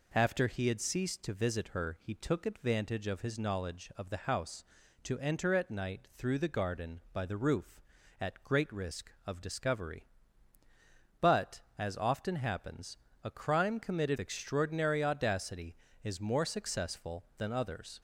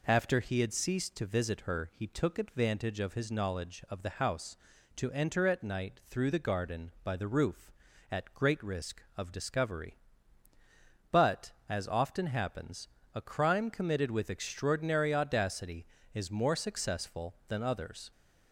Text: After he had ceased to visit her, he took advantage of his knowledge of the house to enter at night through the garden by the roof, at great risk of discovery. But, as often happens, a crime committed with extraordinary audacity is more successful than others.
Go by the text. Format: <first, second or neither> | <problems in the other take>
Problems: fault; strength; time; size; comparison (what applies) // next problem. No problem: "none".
second | skips "with"; at 14.1 s